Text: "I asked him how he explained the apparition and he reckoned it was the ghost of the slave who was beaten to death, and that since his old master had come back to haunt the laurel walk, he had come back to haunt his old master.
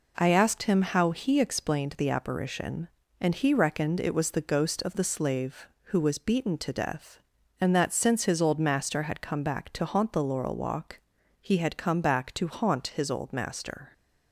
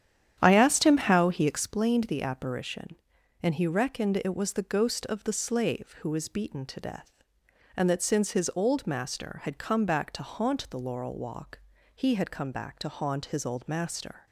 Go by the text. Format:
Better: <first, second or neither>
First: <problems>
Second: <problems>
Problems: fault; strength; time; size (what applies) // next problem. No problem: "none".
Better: first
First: none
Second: starts louder than the rest; strong; until 1.7 s; 10 dB